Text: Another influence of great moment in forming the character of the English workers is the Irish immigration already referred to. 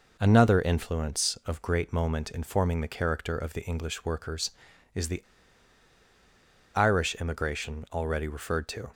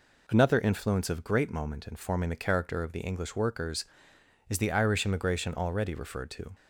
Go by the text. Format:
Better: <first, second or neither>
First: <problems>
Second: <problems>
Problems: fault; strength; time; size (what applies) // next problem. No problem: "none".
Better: second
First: pauses between "the" and "Irish"; strong; at 5.2 s; 1.5 s long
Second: none